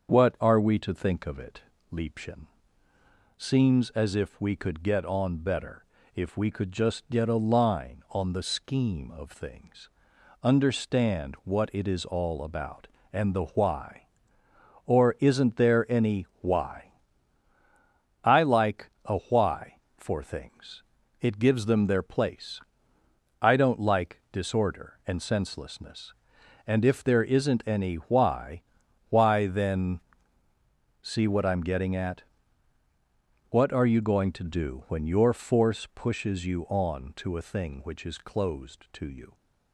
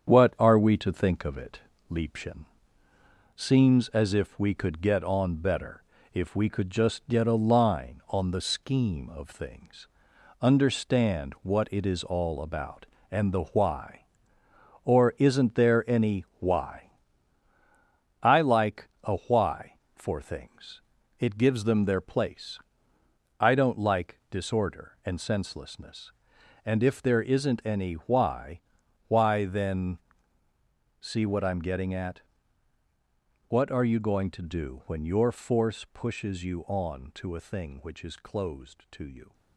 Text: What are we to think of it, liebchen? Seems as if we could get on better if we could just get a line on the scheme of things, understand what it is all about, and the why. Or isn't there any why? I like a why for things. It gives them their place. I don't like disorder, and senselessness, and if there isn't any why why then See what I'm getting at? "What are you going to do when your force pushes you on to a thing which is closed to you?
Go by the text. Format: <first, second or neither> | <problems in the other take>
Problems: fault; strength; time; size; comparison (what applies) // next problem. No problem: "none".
first | gets quieter; noticeable; throughout; 5 dB // starts louder than the rest; strong; until 1.1 s; 8 dB; also in the first // pauses between "better" and "if"; slight; at 5.8 s; 0.32 s long; slight in the first // pauses between "why" and "why"; noticeable; at 28.6 s; 0.46 s long; noticeable in the first // pauses between "then" and "See"; at 29.9 s; 1.0 s long; also in the first